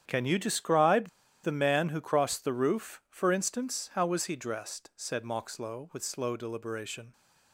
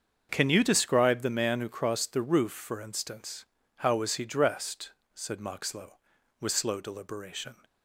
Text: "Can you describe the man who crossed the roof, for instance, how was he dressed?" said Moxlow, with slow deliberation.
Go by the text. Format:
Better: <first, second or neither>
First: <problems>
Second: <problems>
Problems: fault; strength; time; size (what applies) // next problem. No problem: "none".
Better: second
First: starts louder than the rest; strong; until 1.0 s; 9 dB // pauses between "describe" and "the"; slight; at 1.0 s; 0.34 s long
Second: starts louder than the rest; until 1.3 s; 7 dB